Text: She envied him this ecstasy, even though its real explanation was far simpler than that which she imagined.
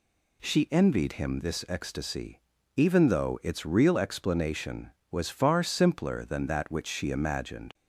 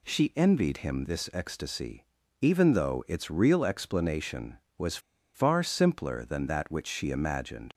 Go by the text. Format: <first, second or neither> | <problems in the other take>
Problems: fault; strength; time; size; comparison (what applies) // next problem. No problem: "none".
first | pauses between "was" and "far"; at 4.9 s; 0.36 s long